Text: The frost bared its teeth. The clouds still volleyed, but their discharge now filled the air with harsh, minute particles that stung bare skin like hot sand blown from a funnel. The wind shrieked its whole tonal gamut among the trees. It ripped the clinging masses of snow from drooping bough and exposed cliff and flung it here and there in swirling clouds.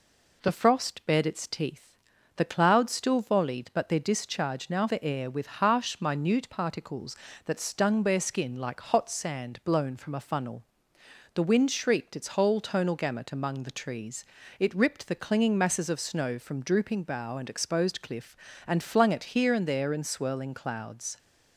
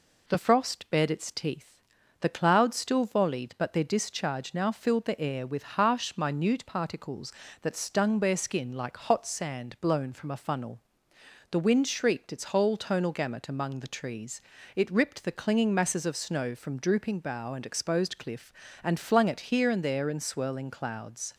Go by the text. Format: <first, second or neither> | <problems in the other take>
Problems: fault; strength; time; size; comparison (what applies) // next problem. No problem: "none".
second | skips "filled"; at 4.8 s